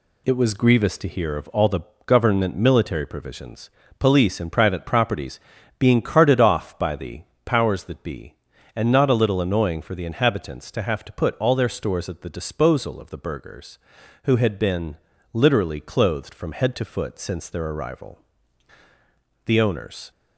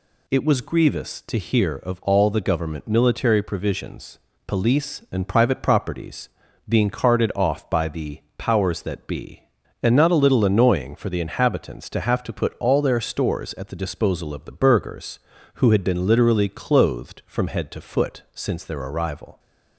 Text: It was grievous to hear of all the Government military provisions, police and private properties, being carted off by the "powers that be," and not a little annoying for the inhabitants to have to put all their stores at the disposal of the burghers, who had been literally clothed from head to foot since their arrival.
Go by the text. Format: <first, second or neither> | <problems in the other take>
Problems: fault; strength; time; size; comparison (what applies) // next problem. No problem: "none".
second | pauses between "the" and "Government"; slight; at 1.8 s; 0.26 s long // pauses between "the" and "powers"; slight; at 7.2 s; 0.22 s long; slight in the second // pauses between "been" and "literally"; slight; at 14.9 s; 0.36 s long // goes on to say "The owners"; noticeable; from 19.4 s on; 0.66 s long